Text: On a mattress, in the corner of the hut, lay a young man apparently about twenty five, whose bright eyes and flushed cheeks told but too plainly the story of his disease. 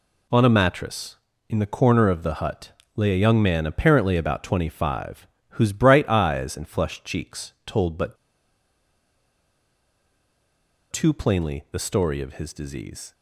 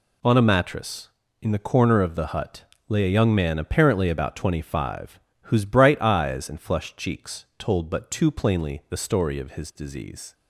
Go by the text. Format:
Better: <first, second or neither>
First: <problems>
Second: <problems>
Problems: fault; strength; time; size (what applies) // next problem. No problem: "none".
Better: second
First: pauses between "but" and "too"; strong; at 8.1 s; 2.7 s long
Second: none